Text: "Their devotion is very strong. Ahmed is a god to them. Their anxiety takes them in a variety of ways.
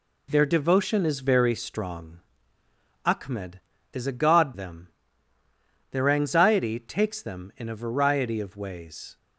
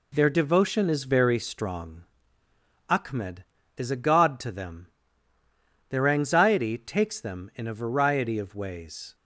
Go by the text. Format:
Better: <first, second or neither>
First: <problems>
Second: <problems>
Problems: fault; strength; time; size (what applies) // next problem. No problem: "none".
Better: second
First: skips "to"; at 4.5 s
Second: none